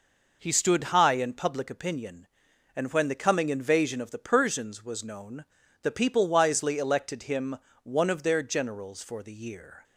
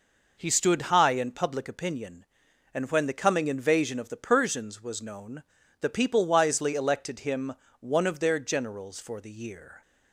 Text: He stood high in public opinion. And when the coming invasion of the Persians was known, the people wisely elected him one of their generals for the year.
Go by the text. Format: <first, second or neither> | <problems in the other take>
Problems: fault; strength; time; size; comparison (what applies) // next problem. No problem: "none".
neither | pauses between "him" and "one"; slight; the same in both